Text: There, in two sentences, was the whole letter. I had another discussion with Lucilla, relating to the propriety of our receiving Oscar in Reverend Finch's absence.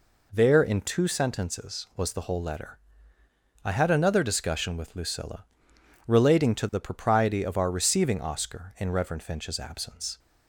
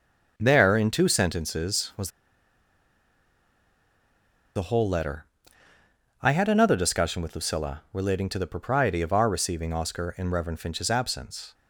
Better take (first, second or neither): first